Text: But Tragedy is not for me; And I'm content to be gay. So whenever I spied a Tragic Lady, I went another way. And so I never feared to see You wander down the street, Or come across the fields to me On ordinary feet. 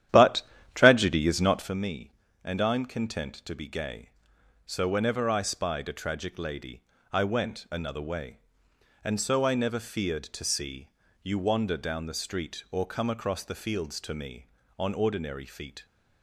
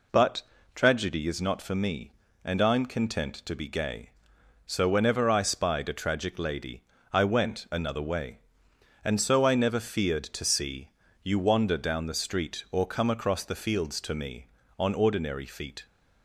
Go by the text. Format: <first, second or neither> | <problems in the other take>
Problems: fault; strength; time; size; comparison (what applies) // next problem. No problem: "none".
second | starts louder than the rest; strong; until 1.7 s; 11 dB // pauses between "But" and "Tragedy"; slight; at 0.4 s; 0.34 s long; slight in the second // pauses between "see" and "You"; slight; at 10.8 s; 0.32 s long; slight in the second